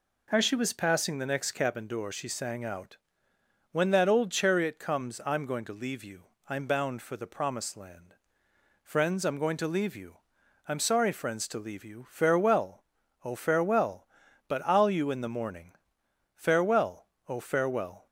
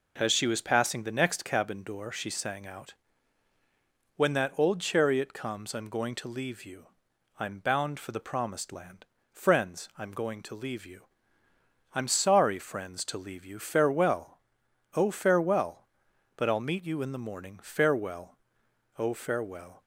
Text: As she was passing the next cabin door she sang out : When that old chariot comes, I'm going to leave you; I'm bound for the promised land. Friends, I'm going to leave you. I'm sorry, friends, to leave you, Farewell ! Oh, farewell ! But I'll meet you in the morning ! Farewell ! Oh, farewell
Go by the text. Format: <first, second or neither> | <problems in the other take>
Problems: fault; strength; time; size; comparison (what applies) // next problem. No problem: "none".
second | skips "meet"; at 14.9 s